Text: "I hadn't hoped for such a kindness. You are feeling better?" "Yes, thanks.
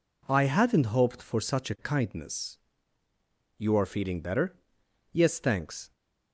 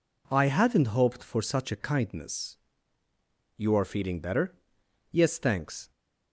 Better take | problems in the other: neither | none

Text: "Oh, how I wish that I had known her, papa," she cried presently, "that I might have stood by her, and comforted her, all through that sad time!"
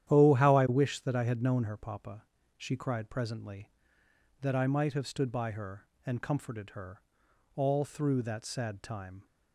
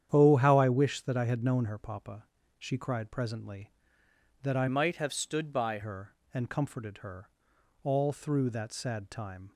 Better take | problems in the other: first | starts louder than the rest; strong; until 1.1 s; 9.5 dB; strong in the first // changes voice from "might" to "by"; from 4.6 to 5.7 s; 1.1 s long

